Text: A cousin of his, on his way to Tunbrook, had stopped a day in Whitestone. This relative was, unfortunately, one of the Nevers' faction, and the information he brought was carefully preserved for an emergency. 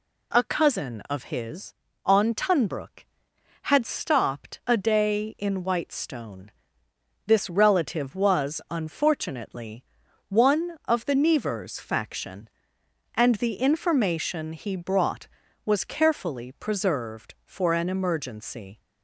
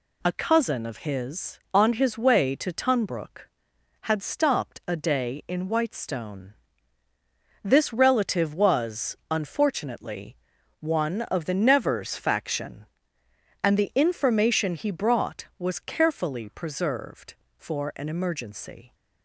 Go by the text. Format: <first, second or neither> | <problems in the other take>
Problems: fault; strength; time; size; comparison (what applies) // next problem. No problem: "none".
second | skips "his way to"; at 2.3 s